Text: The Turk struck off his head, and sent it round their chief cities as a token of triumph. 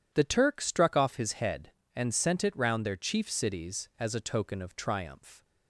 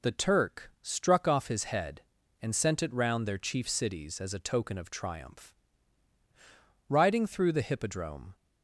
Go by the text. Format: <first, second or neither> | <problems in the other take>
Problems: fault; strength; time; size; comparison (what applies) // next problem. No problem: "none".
first | goes on to say "Riding through the hippodrome"; from 6.8 s on; 1.4 s long